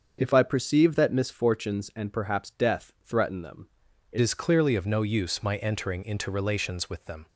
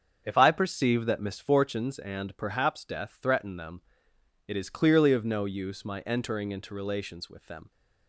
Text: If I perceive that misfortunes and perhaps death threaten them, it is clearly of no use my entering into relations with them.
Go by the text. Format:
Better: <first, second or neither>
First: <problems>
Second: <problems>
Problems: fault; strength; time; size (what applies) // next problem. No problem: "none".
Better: second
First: starts louder than the rest; until 1.2 s; 6.5 dB // changes voice at "is"; from 4.1 s on; 3.1 s long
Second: starts louder than the rest; strong; until 1.2 s; 7 dB